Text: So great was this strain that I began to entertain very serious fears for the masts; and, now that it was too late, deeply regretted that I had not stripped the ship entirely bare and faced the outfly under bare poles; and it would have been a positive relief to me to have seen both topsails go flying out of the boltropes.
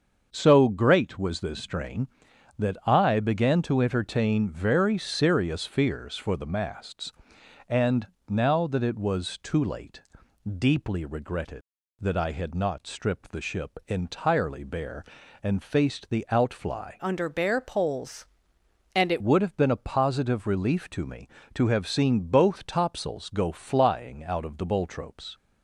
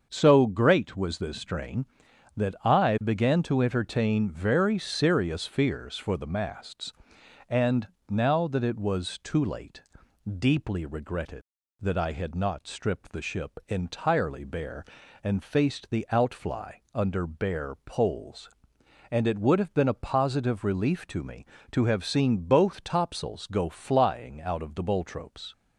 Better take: second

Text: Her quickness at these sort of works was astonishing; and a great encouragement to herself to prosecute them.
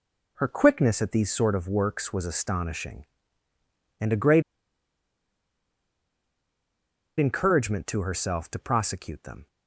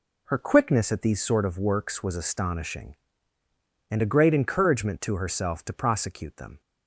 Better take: second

